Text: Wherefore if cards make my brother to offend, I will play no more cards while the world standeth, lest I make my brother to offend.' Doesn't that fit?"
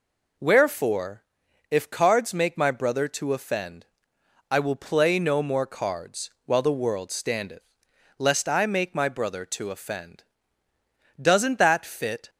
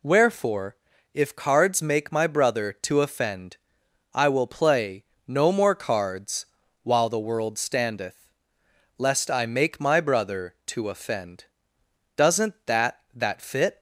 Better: first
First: pauses between "Wherefore" and "if"; noticeable; at 1.2 s; 0.46 s long // pauses between "cards" and "while"; slight; at 6.2 s; 0.16 s long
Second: pauses between "Wherefore" and "if"; at 0.7 s; 0.38 s long // pauses between "play" and "no"; slight; at 5.0 s; 0.24 s long // pauses between "cards" and "while"; at 6.4 s; 0.38 s long // says "that" twice; at 13.1 s

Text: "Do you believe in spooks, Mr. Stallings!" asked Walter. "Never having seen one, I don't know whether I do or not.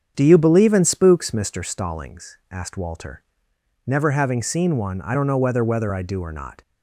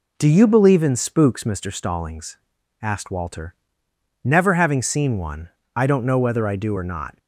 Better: second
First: starts louder than the rest; strong; until 1.1 s; 7.5 dB // says "whether" twice; at 5.6 s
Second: none

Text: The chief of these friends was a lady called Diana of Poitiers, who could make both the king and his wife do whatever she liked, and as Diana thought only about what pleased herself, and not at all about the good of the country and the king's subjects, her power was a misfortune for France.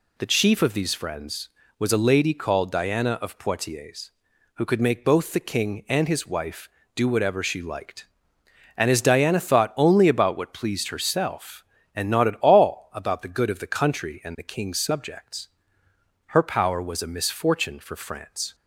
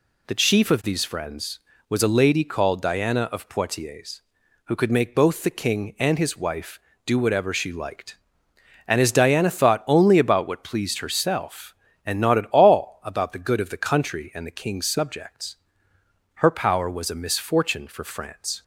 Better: neither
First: none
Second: none

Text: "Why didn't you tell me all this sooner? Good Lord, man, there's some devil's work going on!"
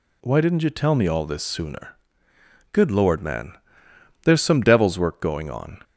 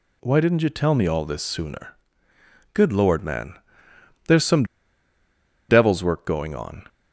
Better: first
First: none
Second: pauses between "some" and "devil's"; at 4.6 s; 1.0 s long

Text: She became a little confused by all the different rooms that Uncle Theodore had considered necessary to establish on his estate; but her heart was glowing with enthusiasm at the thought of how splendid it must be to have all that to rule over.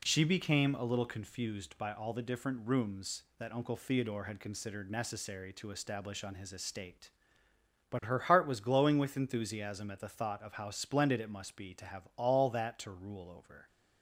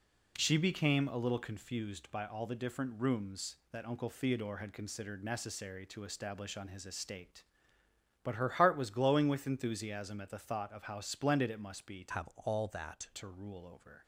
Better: first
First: none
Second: changes voice from "have" to "that"; from 12.1 to 13.1 s; 1.0 s long

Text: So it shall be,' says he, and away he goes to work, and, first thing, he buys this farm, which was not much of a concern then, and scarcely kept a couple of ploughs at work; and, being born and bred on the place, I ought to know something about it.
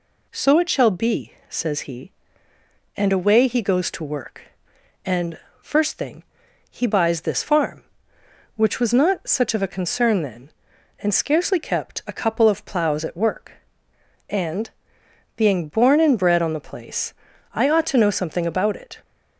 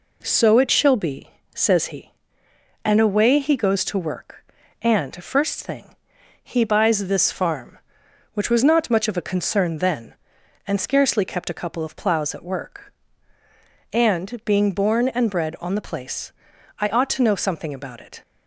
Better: second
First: says "such" for "much"; at 9.2 s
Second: none

